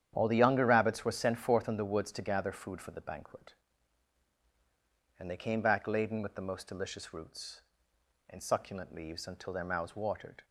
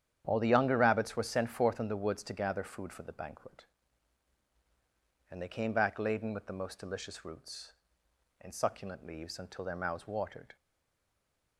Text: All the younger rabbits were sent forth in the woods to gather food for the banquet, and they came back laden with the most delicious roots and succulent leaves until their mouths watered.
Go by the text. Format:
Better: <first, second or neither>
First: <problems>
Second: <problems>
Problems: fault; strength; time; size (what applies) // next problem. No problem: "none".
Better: first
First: starts louder than the rest; strong; until 1.1 s; 9.5 dB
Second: starts louder than the rest; strong; until 1.2 s; 9.5 dB // stays silent after the last word; from 10.5 s on; 1.0 s long